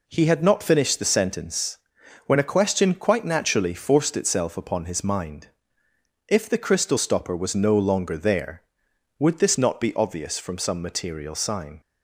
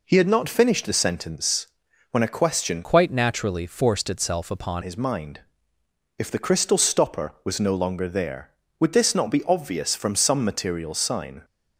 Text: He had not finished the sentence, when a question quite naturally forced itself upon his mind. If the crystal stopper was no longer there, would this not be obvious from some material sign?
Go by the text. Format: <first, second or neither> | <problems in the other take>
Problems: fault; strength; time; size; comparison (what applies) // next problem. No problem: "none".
first | changes voice from "quite" to "upon"; from 2.8 to 4.8 s; 2.0 s long